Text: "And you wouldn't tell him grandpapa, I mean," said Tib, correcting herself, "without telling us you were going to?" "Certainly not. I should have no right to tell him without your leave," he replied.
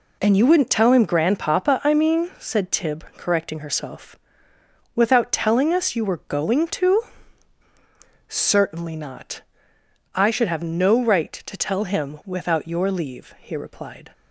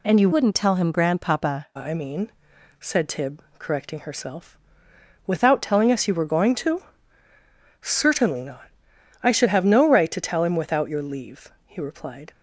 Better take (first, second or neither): first